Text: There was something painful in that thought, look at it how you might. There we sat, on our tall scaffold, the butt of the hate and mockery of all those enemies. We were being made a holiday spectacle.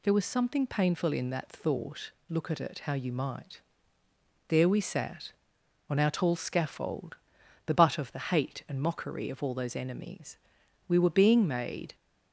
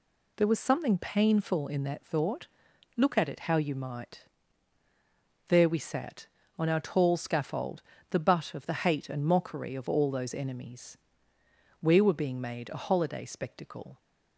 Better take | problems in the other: second | stops before "a holiday spectacle"; at 11.9 s

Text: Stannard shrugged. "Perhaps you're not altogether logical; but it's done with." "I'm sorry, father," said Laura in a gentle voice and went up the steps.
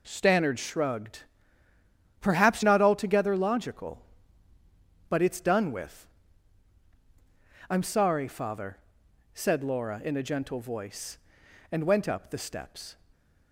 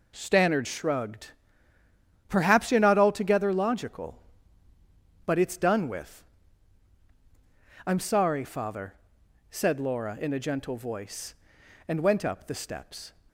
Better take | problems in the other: second | skips "you're"; at 2.6 s

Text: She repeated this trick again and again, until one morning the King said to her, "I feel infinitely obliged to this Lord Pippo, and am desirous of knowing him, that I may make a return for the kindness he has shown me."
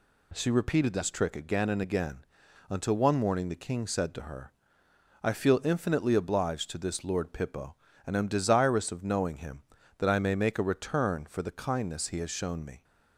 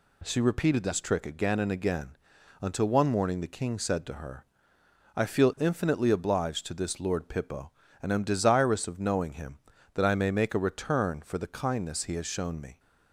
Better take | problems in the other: neither | none

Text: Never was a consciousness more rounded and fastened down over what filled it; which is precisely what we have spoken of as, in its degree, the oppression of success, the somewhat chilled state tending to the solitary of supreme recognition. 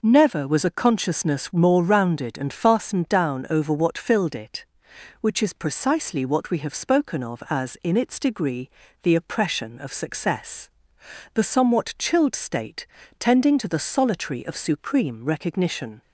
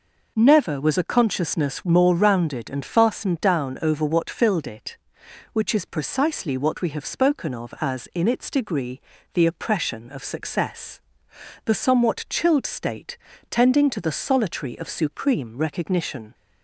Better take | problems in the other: neither | pauses between "state" and "tending"; slight; the same in both

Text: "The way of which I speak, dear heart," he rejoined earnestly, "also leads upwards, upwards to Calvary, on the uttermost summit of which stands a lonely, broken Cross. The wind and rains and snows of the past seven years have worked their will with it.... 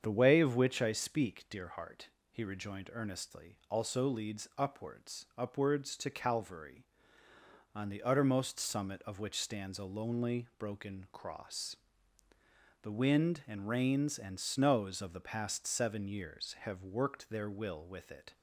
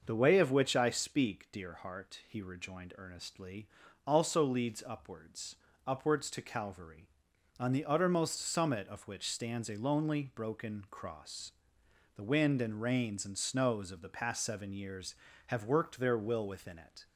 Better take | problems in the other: first | starts louder than the rest; noticeable; until 1.0 s; 6 dB; strong in the first // says "within" for "with"; at 16.4 s

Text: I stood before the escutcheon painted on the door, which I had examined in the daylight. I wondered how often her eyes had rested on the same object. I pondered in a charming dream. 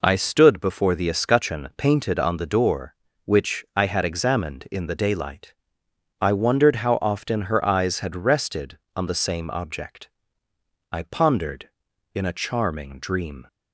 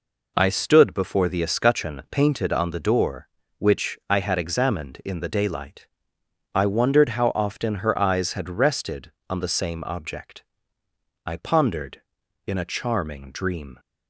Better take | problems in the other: neither | none

